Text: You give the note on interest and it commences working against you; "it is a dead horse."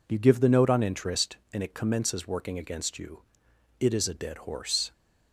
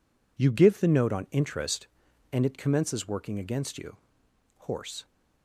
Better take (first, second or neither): first